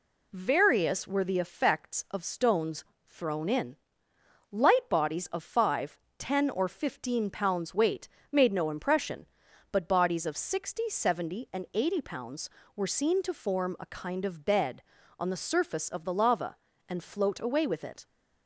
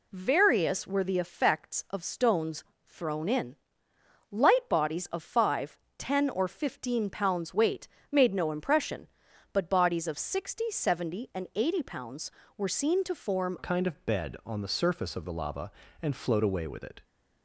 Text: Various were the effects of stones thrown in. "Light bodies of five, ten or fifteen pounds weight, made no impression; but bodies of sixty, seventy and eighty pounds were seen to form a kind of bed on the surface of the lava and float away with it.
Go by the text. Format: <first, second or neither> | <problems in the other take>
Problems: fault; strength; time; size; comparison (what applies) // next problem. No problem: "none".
first | pauses between "stones" and "thrown"; slight; at 2.6 s; 0.20 s long; slight in the first // changes voice at "a"; from 13.5 s on; 3.5 s long